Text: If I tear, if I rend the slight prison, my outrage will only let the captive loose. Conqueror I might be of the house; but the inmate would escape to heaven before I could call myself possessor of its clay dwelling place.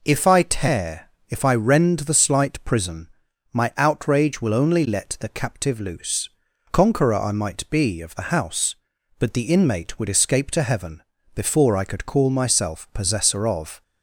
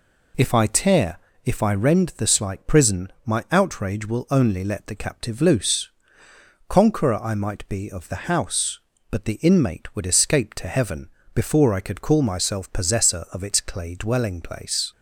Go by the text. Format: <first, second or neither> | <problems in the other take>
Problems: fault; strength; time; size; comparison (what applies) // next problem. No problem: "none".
second | pauses between "heaven" and "before"; slight; at 11.0 s; 0.32 s long; slight in the second // stops before "its clay dwelling place"; at 13.8 s